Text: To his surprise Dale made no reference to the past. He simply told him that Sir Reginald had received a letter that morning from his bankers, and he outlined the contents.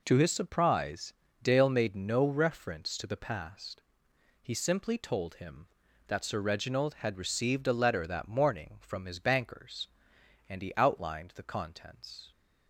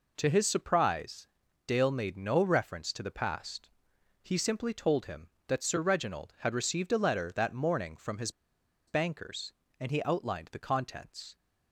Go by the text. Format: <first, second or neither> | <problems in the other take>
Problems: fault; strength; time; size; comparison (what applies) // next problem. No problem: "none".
first | pauses between "surprise" and "Dale"; at 1.2 s; 0.40 s long; slight in the first // pauses between "his" and "bankers"; noticeable; at 8.2 s; 0.58 s long